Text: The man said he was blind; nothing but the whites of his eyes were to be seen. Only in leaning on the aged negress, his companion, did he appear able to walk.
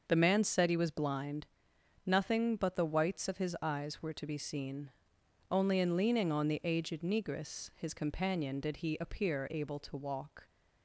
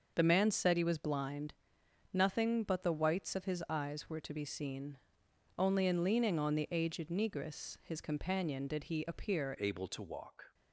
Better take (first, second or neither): first